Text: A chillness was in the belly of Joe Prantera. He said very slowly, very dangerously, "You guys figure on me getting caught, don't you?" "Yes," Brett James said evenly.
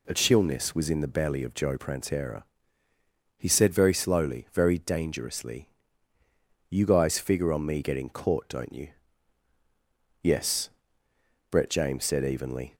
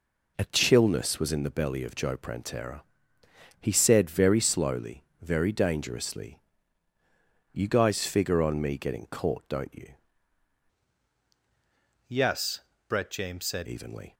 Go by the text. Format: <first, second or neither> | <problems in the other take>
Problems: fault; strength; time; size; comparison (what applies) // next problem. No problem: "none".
first | changes voice from "Yes" to "said"; from 12.0 to 13.6 s; 1.6 s long